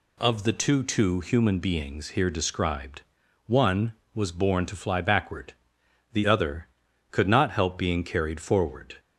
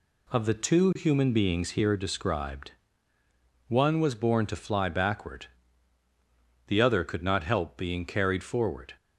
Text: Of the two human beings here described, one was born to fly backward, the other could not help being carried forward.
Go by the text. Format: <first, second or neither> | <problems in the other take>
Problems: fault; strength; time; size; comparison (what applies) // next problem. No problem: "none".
second | says "two" twice; at 0.8 s